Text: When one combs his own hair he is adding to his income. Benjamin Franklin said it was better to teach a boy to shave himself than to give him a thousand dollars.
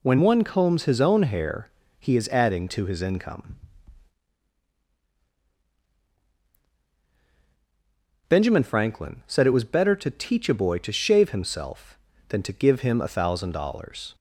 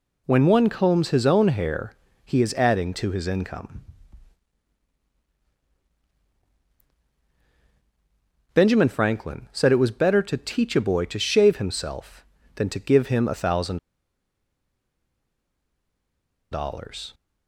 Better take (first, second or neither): first